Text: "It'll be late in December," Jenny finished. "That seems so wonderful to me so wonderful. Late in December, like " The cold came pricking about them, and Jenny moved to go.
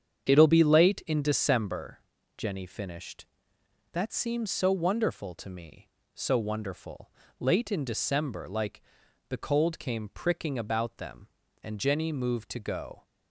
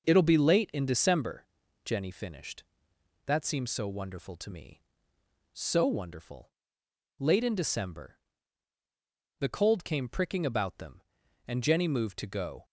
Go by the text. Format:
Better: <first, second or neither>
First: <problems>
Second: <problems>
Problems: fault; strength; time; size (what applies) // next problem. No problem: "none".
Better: first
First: starts louder than the rest; strong; until 1.2 s; 8 dB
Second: starts louder than the rest; until 1.1 s; 7 dB // skips "like"; at 8.4 s